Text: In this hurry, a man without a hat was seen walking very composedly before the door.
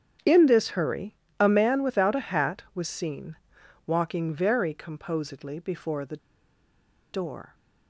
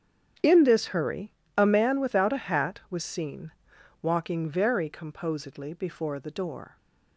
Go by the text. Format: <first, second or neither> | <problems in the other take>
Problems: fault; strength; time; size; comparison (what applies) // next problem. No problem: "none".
second | starts louder than the rest; strong; until 1.5 s; 8.5 dB; strong in the second // pauses between "seen" and "walking"; noticeable; at 3.3 s; 0.50 s long; noticeable in the second // pauses between "the" and "door"; noticeable; at 6.1 s; 0.93 s long